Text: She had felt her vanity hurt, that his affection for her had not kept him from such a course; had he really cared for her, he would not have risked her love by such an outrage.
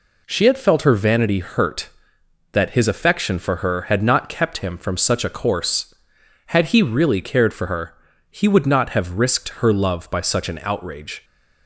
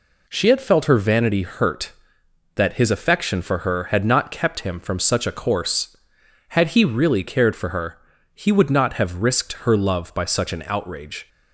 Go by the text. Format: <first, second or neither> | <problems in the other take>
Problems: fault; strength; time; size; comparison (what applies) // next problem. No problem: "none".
neither | none